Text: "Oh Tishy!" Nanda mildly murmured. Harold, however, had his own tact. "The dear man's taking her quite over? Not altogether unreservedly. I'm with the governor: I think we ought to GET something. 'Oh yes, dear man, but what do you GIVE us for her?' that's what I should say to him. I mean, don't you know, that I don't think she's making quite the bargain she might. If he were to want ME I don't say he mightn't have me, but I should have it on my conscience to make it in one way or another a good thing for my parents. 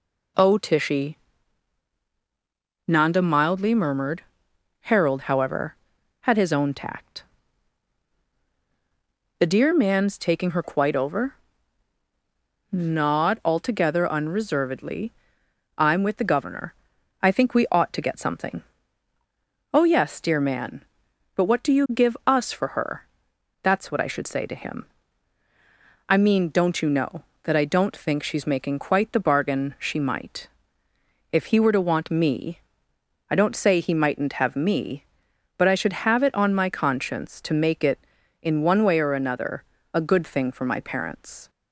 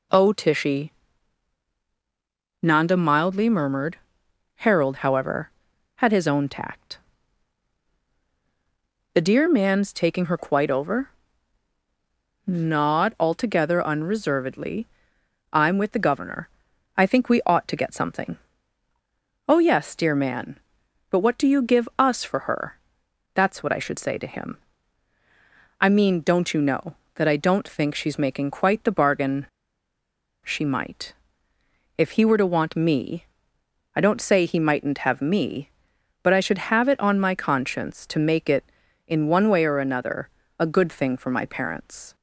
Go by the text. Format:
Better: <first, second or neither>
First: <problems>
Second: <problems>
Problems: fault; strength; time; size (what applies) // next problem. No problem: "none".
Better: first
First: pauses between "ME" and "I"; noticeable; at 32.6 s; 0.68 s long // pauses between "another" and "a"; slight; at 39.6 s; 0.30 s long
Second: pauses between "bargain" and "she"; noticeable; at 29.4 s; 0.97 s long // pauses between "ME" and "I"; noticeable; at 33.2 s; 0.68 s long // pauses between "another" and "a"; slight; at 40.2 s; 0.30 s long